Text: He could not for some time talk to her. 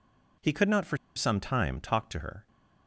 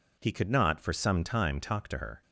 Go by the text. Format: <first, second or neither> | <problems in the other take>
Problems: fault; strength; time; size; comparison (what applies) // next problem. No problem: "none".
second | pauses between "for" and "some"; slight; at 0.9 s; 0.19 s long